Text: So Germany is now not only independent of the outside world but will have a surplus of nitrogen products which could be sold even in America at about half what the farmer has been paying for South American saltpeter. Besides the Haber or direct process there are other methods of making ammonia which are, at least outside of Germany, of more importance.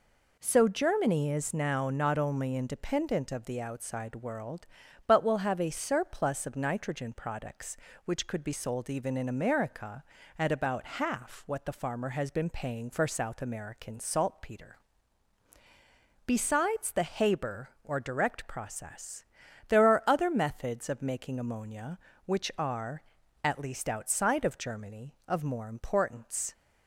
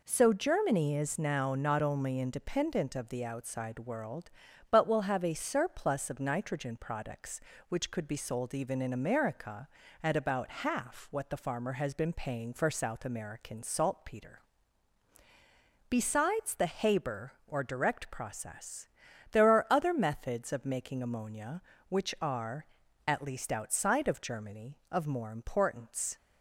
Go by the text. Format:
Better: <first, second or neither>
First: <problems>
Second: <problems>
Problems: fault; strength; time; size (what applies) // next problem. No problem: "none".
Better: neither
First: pauses between "process" and "there"; at 19.2 s; 0.44 s long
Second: pauses between "process" and "there"; at 18.8 s; 0.44 s long